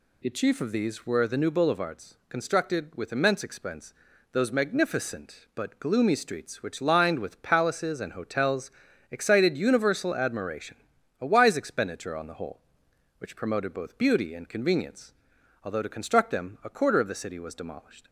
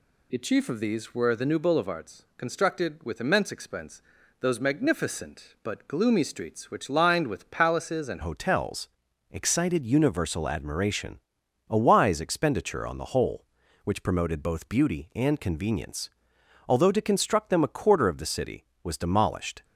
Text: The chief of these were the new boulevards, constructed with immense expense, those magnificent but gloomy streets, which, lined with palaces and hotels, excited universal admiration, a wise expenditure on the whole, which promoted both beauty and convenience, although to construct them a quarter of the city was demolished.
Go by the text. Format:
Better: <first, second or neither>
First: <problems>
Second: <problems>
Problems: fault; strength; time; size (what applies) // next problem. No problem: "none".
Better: first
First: none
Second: changes voice at "hotels"; from 8.2 s on; 11.4 s long